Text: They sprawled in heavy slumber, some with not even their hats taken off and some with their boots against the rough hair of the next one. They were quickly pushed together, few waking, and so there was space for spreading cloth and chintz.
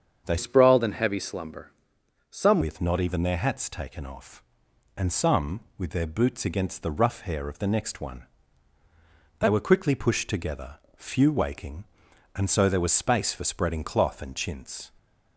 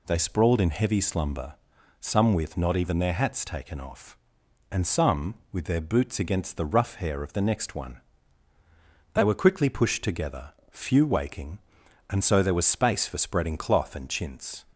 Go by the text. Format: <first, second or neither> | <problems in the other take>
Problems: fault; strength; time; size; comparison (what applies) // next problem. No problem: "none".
second | starts louder than the rest; strong; until 1.2 s; 7.5 dB // changes voice from "sprawled" to "some"; from 0.3 to 2.5 s; 2.2 s long